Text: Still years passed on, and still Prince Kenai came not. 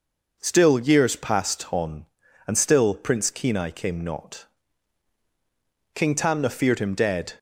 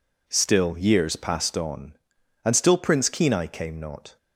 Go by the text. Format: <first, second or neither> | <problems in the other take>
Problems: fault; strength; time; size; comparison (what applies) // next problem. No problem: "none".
second | goes on to say "King Tamna feared him dead"; from 5.9 s on; 1.4 s long